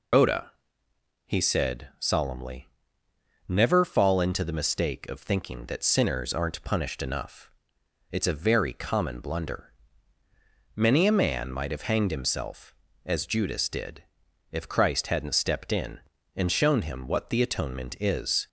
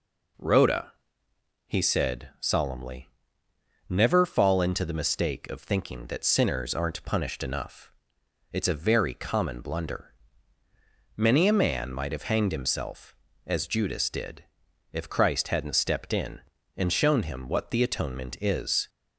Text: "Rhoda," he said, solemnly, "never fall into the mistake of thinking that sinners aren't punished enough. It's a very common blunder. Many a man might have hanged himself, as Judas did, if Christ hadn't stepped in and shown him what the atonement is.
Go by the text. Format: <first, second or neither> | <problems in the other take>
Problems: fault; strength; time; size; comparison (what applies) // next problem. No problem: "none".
second | loses the start of "Rhoda"; at 0.1 s; 170 ms